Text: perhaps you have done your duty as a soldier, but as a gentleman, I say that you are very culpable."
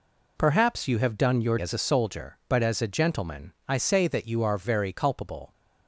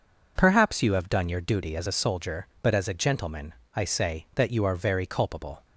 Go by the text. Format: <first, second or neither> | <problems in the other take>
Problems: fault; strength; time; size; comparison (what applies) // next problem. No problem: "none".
second | skips "duty"; at 1.5 s